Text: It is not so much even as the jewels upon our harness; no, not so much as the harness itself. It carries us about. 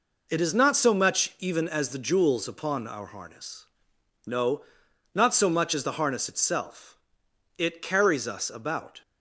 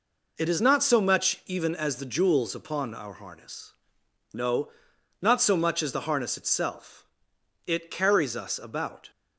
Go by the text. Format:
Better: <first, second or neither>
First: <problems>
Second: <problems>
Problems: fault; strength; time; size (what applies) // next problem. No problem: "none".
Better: neither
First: none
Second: none